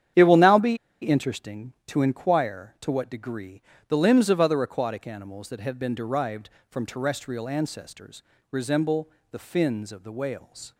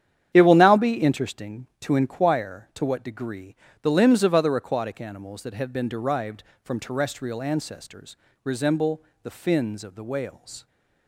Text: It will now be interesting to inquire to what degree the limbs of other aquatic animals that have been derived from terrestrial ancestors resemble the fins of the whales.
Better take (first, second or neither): second